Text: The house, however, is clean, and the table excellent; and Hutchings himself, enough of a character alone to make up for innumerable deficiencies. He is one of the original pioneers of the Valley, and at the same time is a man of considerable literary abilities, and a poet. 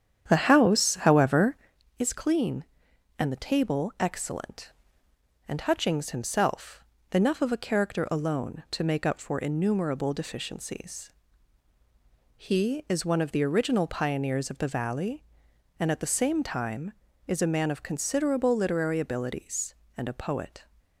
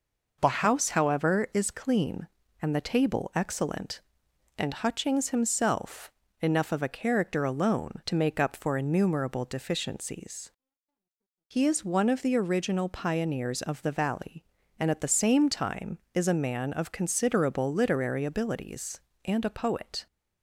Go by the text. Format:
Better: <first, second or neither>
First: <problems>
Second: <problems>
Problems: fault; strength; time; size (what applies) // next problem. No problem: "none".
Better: second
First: starts louder than the rest; strong; until 1.8 s; 9 dB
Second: none